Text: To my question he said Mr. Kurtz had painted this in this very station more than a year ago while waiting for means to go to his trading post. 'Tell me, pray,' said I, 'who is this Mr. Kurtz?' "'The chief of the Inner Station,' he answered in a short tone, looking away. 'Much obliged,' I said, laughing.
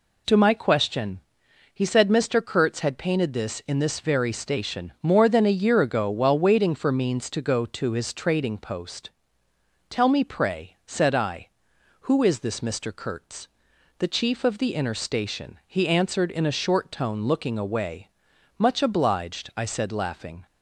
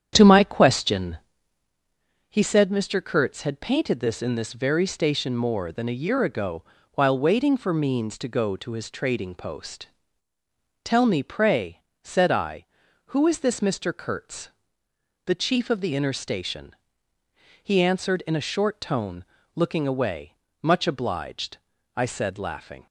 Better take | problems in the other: first | starts louder than the rest; strong; until 1.7 s; 9 dB // pauses between "question" and "he"; at 1.1 s; 1.1 s long; noticeable in the first // pauses between "ago" and "while"; slight; at 6.6 s; 0.32 s long

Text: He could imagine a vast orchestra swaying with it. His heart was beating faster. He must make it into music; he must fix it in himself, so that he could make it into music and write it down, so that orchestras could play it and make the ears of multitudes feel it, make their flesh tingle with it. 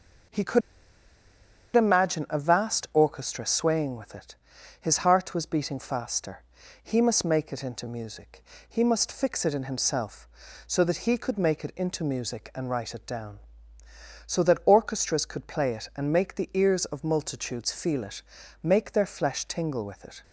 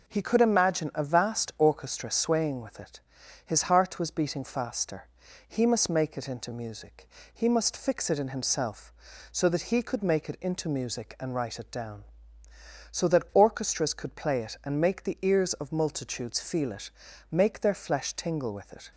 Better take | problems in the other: second | pauses between "could" and "imagine"; at 0.6 s; 1.1 s long

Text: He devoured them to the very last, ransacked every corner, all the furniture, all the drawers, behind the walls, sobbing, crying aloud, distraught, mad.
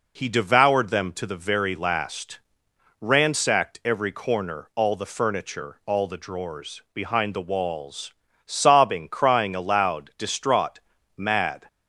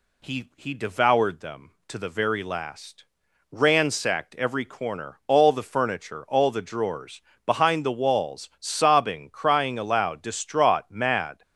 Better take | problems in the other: first | says "He" twice; at 0.5 s

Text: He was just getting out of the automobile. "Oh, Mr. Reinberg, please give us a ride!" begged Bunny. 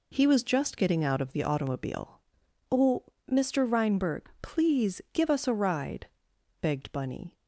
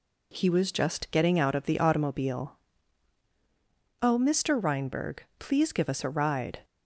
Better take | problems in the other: first | stops before "begged Bunny"; at 6.6 s

